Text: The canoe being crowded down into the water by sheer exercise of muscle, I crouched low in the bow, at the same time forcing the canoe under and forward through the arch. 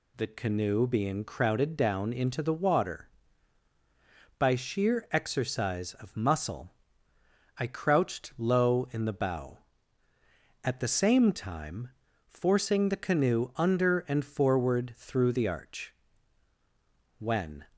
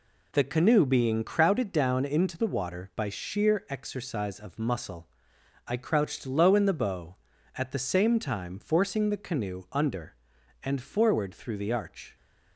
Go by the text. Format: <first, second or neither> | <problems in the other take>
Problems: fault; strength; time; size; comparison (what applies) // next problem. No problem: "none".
second | pauses between "time" and "forcing"; at 11.8 s; 0.38 s long // goes on to say "When"; slight; from 17.1 s on; 0.46 s long